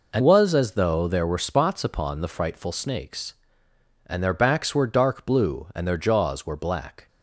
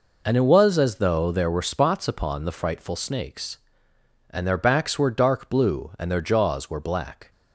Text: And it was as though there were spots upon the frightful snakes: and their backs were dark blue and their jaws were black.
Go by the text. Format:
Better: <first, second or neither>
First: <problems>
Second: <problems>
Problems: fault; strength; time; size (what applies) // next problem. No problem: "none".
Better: second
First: skips "it"; at 0.2 s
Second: none